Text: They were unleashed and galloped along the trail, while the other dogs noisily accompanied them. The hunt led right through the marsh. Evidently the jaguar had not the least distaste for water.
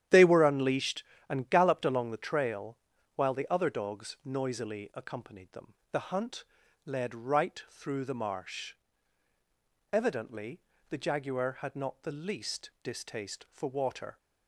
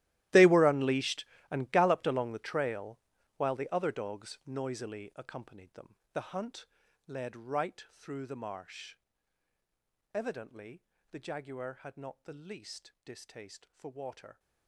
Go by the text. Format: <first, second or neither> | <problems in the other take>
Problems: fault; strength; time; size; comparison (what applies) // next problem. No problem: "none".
first | gets quieter; strong; throughout; 18 dB // starts louder than the rest; strong; until 1.5 s; 15 dB; strong in the first // pauses between "hunt" and "led"; at 6.6 s; 0.40 s long; also in the first // pauses between "Evidently" and "the"; slight; at 10.8 s; 0.30 s long; slight in the first